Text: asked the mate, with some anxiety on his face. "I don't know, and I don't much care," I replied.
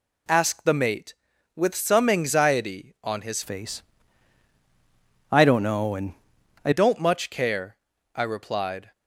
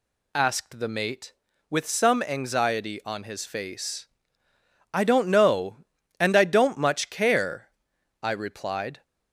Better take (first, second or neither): second